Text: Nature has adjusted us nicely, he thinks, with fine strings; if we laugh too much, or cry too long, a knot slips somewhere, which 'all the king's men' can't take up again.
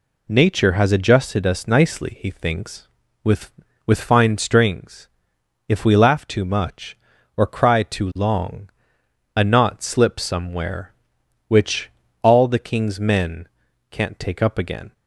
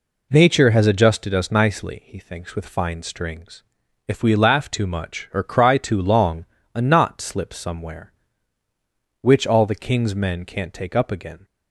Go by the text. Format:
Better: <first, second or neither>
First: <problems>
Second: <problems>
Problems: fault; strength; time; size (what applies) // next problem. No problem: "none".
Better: second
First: says "with" twice; at 3.8 s // pauses between "which" and "all"; slight; at 11.9 s; 0.32 s long // pauses between "men" and "can't"; at 13.4 s; 0.42 s long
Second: none